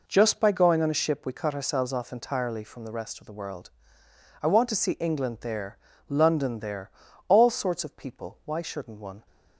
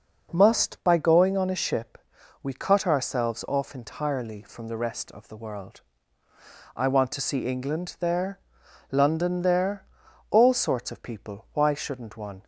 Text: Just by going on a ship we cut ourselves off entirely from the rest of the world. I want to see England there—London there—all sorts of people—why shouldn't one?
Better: first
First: none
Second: says "Must" for "Just"; at 0.3 s // pauses between "ship" and "we"; noticeable; at 1.9 s; 0.46 s long

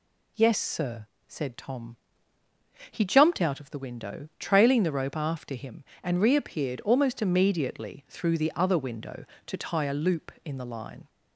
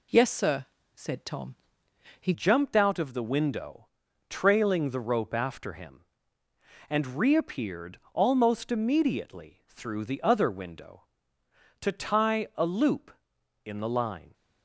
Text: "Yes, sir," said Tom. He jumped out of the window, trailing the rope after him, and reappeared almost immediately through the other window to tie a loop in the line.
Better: first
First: none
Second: changes voice at "jumped"; from 2.3 s on; 12.0 s long // pauses between "reappeared" and "almost"; slight; at 7.9 s; 0.16 s long

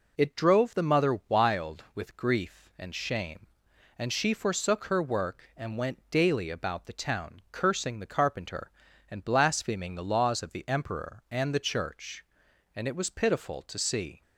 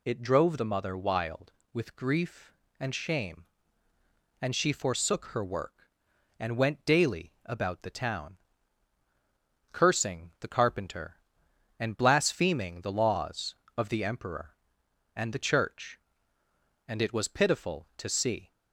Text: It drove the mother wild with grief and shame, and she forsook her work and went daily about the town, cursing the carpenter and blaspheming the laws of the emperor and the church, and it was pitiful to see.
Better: neither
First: none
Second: none

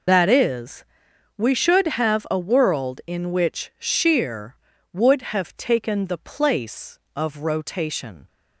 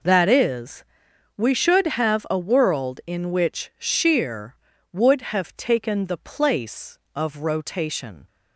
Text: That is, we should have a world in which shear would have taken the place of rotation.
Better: second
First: loses the start of "That"; at 0.0 s; 50 ms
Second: none

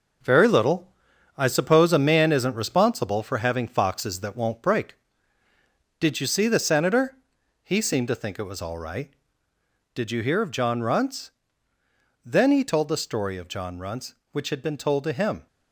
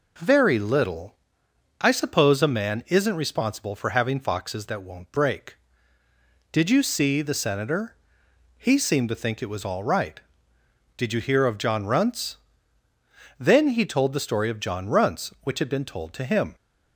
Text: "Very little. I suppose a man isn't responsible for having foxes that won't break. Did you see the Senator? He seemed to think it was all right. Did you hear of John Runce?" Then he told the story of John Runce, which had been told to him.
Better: second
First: gets quieter; throughout; 6.5 dB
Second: none

